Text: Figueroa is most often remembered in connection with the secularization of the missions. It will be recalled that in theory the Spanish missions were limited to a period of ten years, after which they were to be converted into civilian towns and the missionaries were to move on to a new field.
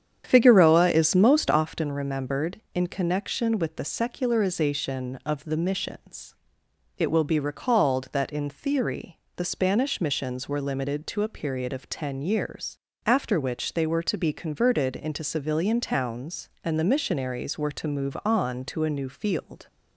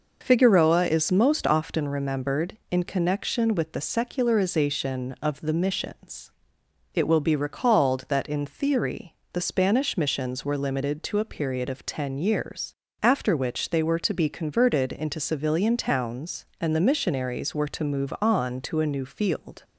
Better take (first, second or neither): second